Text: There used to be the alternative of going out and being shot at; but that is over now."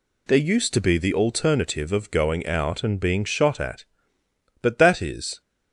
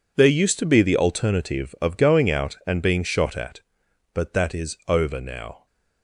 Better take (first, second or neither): second